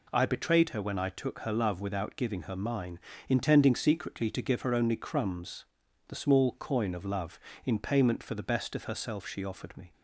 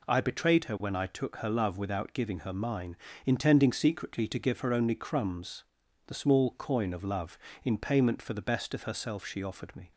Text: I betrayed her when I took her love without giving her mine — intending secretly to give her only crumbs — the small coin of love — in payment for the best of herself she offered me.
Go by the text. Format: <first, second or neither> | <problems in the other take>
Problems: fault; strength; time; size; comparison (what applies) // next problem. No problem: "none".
neither | none